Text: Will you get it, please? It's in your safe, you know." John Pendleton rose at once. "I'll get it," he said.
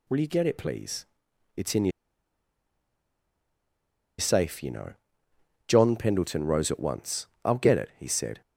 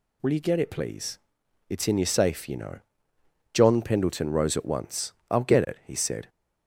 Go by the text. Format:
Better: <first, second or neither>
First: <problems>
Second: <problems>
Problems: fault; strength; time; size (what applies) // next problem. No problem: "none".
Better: second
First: pauses between "your" and "safe"; strong; at 1.9 s; 2.3 s long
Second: none